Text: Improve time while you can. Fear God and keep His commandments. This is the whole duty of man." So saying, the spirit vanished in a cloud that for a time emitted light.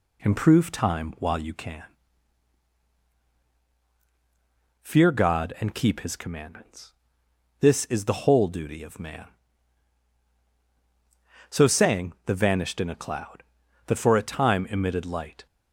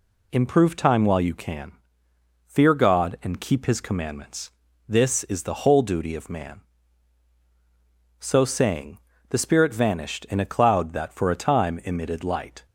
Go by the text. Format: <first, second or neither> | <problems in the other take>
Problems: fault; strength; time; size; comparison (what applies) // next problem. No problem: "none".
second | skips "spirit"; at 12.3 s